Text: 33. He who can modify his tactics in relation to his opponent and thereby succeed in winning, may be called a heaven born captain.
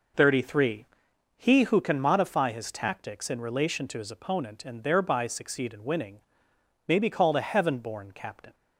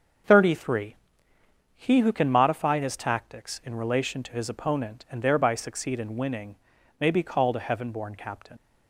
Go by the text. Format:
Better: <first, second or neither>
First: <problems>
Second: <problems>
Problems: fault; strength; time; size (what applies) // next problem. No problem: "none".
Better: first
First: none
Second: starts louder than the rest; until 2.0 s; 6.5 dB // leaves "captain" unfinished; at 8.5 s; 75 ms